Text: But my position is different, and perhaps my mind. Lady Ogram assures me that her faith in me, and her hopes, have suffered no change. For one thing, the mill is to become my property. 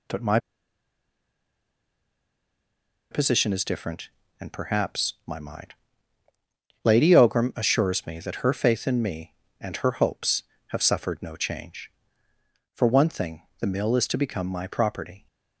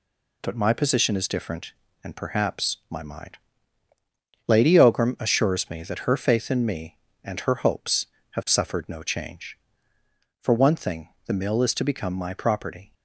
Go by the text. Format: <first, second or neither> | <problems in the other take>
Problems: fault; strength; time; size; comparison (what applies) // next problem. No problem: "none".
second | pauses between "my" and "position"; strong; at 0.3 s; 2.7 s long